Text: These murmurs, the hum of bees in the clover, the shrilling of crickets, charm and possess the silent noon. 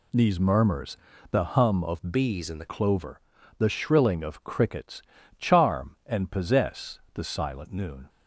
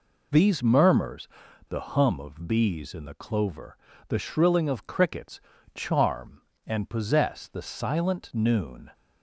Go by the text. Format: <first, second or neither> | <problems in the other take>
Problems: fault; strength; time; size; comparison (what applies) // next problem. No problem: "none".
second | changes voice from "bees" to "the"; from 2.1 to 2.6 s; 0.5 s long